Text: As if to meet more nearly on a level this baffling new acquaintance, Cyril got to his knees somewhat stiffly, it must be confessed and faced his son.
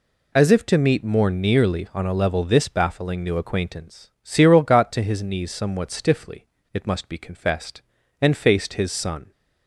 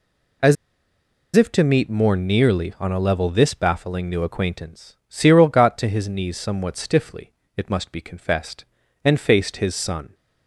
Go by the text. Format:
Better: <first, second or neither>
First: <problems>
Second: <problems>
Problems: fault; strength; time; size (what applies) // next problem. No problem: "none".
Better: first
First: none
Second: pauses between "As" and "if"; noticeable; at 0.5 s; 0.80 s long